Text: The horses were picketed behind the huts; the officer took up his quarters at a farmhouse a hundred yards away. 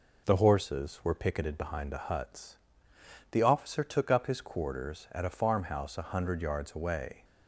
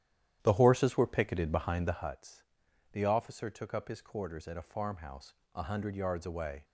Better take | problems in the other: first | starts louder than the rest; strong; until 2.1 s; 11 dB // pauses between "farmhouse" and "a"; slight; at 5.3 s; 0.20 s long

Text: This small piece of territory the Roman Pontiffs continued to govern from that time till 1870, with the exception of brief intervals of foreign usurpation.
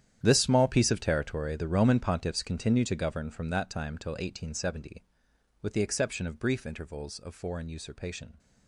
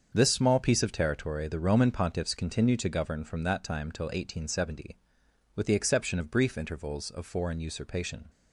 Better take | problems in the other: second | gets quieter; strong; throughout; 15.5 dB // starts louder than the rest; strong; until 1.2 s; 10 dB; also in the second

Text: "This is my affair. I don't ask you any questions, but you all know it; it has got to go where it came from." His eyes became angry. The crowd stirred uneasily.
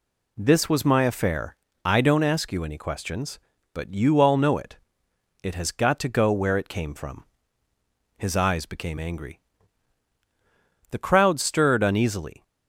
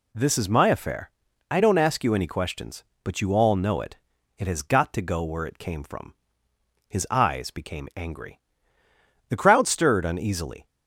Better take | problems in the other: second | says "was" for "is"; at 0.6 s

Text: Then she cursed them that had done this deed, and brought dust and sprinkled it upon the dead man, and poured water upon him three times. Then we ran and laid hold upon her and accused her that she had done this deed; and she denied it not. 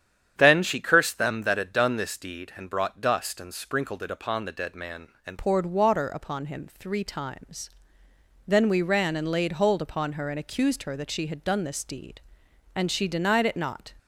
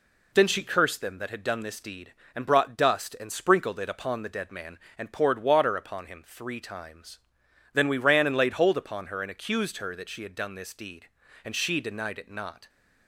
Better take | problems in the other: second | starts louder than the rest; strong; until 1.3 s; 9 dB // changes voice at "poured"; from 5.3 s on; 8.6 s long

